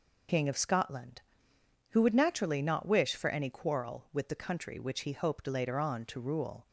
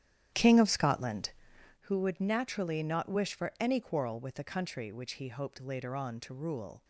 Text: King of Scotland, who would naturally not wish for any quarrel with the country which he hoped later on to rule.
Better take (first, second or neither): first